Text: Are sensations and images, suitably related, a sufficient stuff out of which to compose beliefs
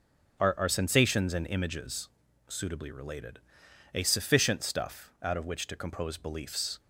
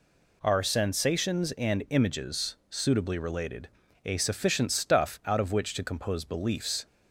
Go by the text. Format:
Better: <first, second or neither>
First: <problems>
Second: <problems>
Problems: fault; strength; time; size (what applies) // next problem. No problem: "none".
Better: second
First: starts louder than the rest; until 1.4 s; 6 dB // says "Are" twice; at 0.5 s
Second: none